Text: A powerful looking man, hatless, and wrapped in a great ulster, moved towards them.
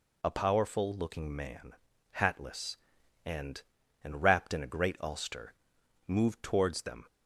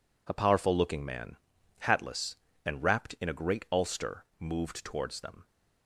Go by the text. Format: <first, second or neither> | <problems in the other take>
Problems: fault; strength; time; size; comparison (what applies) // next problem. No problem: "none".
second | says "and" twice; at 4.0 s